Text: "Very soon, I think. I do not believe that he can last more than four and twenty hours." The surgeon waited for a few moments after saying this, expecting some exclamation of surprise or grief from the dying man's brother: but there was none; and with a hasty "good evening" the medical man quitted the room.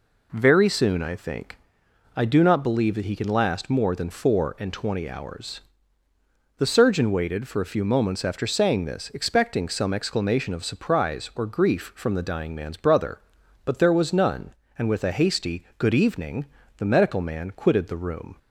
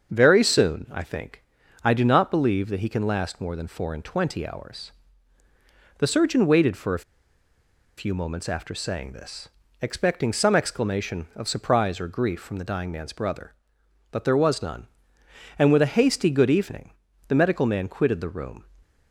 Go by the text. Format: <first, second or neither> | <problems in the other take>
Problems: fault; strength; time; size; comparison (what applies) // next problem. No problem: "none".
first | starts louder than the rest; until 1.1 s; 7 dB // pauses between "a" and "few"; noticeable; at 7.0 s; 0.96 s long // pauses between "evening" and "the"; slight; at 16.9 s; 0.36 s long; slight in the first